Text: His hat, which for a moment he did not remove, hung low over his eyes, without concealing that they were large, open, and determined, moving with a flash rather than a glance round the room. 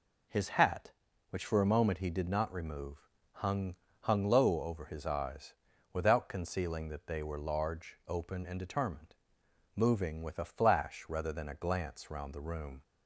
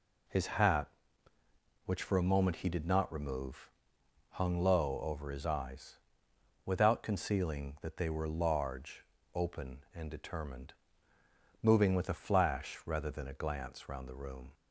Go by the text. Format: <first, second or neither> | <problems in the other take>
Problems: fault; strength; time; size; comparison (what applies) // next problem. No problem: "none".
second | says "hung" twice; at 3.9 s